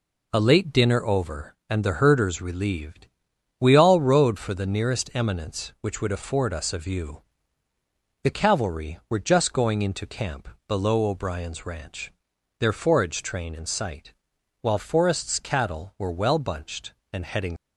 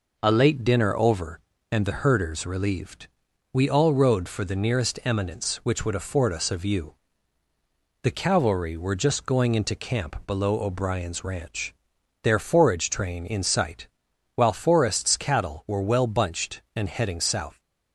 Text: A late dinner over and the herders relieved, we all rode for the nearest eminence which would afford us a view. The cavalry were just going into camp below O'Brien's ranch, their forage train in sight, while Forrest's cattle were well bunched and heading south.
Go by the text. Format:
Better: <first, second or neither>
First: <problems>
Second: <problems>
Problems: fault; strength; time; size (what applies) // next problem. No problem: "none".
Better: second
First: pauses between "camp" and "below"; slight; at 10.4 s; 0.22 s long // stops before "south"; at 17.5 s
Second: none